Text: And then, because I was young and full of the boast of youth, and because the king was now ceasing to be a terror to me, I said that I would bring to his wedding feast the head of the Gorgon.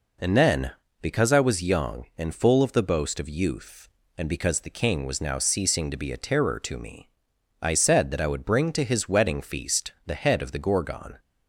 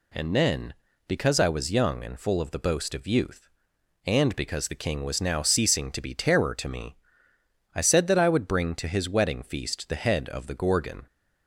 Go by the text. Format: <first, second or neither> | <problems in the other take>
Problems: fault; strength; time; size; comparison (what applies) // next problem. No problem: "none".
first | skips "a"; at 6.1 s